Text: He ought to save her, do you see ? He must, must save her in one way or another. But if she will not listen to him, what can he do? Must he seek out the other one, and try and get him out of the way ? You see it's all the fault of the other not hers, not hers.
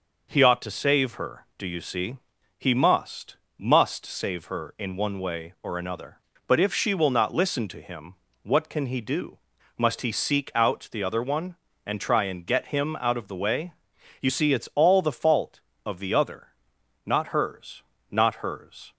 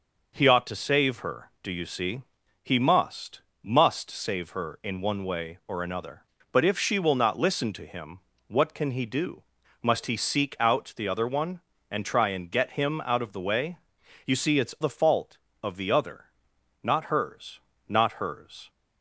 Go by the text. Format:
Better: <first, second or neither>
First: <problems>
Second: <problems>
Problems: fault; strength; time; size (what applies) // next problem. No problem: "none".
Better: first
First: pauses between "other" and "not"; noticeable; at 16.4 s; 0.58 s long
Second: skips "all"; at 14.7 s // pauses between "other" and "not"; noticeable; at 16.2 s; 0.58 s long